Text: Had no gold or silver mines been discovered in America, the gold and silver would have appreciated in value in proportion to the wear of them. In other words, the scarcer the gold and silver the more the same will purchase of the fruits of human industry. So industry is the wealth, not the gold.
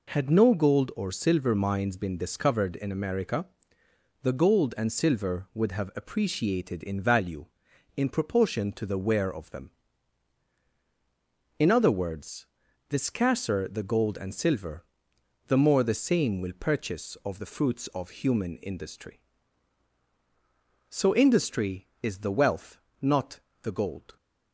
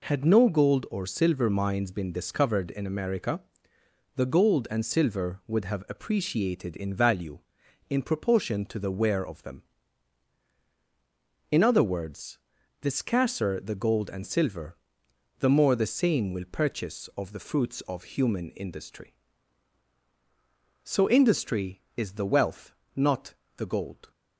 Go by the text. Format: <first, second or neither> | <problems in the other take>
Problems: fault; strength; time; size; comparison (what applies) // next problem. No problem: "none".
neither | pauses between "silver" and "the"; noticeable; the same in both // pauses between "not" and "the"; slight; the same in both